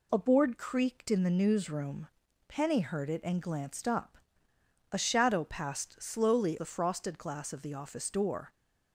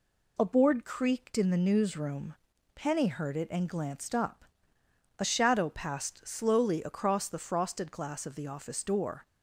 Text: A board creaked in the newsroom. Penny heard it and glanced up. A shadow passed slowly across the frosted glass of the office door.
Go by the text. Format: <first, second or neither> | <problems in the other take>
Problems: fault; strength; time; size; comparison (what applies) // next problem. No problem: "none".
second | skips "across"; at 6.5 s